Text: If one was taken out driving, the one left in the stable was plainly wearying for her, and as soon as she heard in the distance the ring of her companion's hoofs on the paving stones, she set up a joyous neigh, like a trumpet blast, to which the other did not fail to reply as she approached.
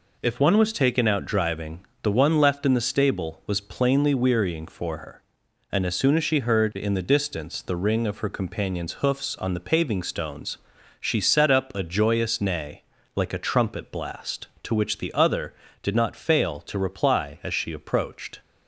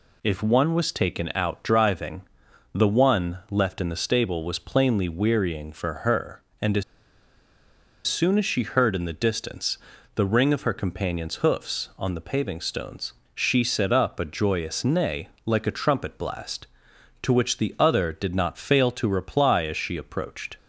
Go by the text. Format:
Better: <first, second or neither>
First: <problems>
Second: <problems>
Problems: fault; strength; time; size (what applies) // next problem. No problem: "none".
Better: first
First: none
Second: pauses between "as" and "soon"; at 6.8 s; 1.2 s long // pauses between "distance" and "the"; slight; at 9.7 s; 0.34 s long